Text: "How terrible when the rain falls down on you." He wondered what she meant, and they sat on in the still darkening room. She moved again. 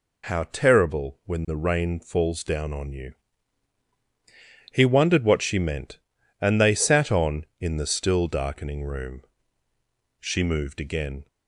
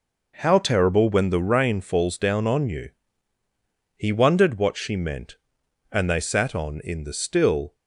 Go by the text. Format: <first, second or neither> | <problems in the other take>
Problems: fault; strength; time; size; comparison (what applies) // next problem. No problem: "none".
first | stops before "darkening room She moved again"; at 7.7 s